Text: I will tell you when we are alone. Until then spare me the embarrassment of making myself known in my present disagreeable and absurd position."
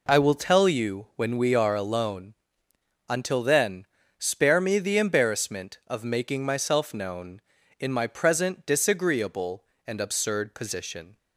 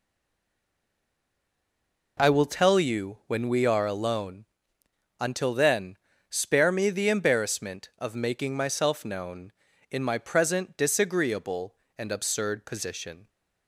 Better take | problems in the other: first | stays silent before the first word; until 2.1 s; 2.1 s long // pauses between "then" and "spare"; slight; at 5.9 s; 0.32 s long; slight in the first

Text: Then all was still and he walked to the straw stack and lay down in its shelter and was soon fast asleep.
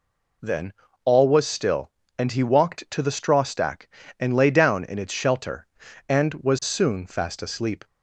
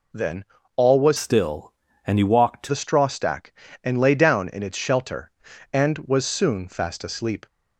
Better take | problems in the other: first | pauses between "Then" and "all"; slight; at 0.4 s; 0.32 s long; slight in the first // changes voice from "still" to "to"; from 1.1 to 2.7 s; 1.6 s long

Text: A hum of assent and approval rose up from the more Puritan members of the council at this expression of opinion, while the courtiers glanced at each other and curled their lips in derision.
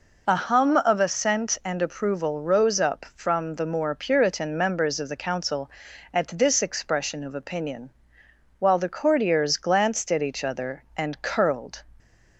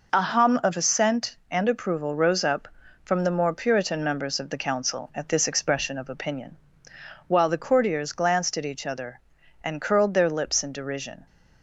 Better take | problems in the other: second | stops before "their lips in derision"; at 12.0 s

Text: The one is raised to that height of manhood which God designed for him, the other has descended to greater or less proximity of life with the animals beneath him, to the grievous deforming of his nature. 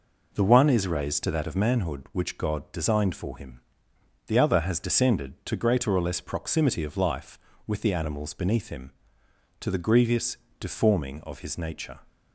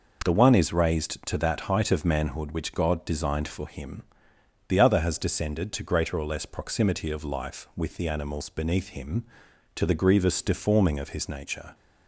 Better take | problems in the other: second | skips "height"; at 1.4 s // pauses between "grievous" and "deforming"; slight; at 10.3 s; 0.20 s long

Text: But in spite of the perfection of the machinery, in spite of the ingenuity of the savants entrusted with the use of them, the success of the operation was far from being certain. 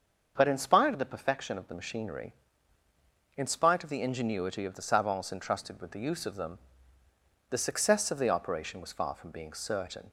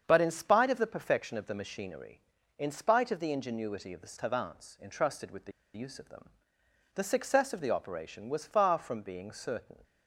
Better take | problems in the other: first | starts louder than the rest; strong; until 1.0 s; 7 dB; also in the first // pauses between "the" and "use"; slight; at 5.5 s; 0.25 s long

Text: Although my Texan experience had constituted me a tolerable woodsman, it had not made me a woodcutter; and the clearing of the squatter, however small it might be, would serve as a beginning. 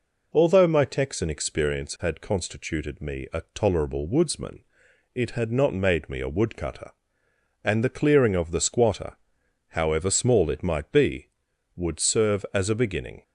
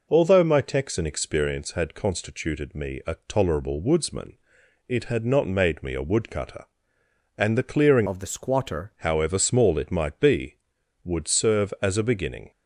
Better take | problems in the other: first | changes voice from "of" to "squatter"; from 8.0 to 8.9 s; 0.9 s long

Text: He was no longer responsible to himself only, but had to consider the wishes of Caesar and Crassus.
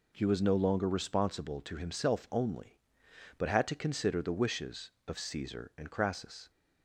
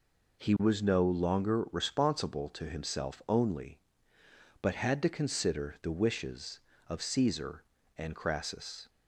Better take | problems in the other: neither | none

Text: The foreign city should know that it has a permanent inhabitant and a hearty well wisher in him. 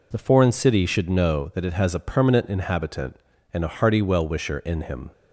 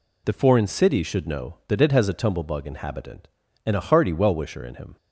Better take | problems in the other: first | says "tumblebug" for "permanent"; at 2.1 s

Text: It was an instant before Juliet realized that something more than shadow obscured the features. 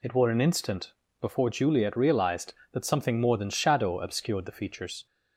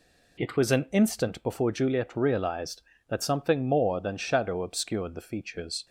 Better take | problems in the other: second | says "were" for "was"; at 0.1 s // pauses between "instant" and "before"; slight; at 0.9 s; 0.28 s long

